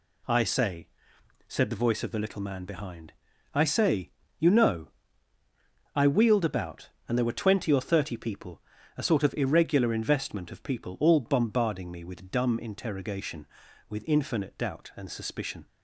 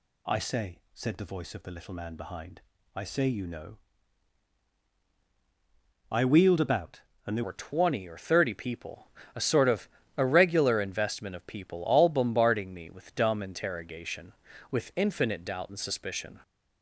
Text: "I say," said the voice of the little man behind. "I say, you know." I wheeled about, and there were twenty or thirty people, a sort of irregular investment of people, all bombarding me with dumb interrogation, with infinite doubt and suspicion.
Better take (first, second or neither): first